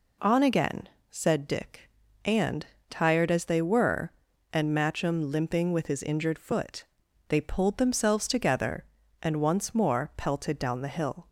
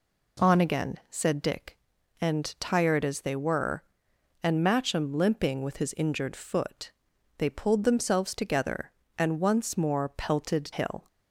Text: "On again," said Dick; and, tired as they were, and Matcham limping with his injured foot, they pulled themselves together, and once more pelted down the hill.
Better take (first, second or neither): first